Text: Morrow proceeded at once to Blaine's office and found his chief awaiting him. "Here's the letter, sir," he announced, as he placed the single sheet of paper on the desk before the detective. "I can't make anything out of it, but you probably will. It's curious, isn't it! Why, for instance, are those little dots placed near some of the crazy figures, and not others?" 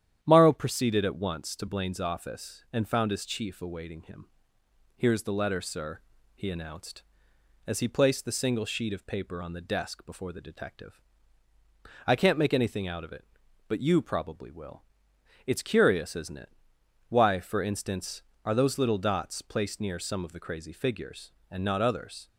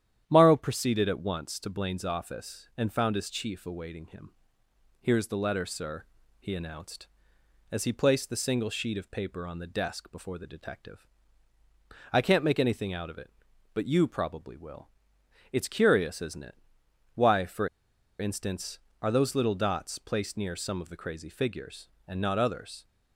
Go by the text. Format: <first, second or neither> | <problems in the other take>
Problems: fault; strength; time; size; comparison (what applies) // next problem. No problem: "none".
first | starts louder than the rest; strong; until 1.2 s; 10 dB; strong in the first // pauses between "for" and "instance"; noticeable; at 17.6 s; 0.51 s long